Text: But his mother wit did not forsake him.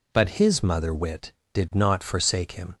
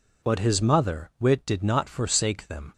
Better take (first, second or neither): first